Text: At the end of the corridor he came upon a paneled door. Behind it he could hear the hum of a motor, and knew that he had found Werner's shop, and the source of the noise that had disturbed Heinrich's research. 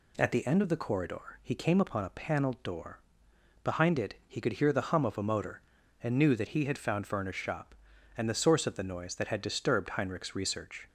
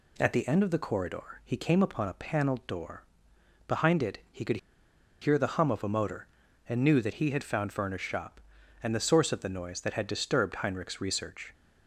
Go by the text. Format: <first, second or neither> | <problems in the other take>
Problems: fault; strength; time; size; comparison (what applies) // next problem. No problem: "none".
first | pauses between "could" and "hear"; noticeable; at 4.5 s; 0.64 s long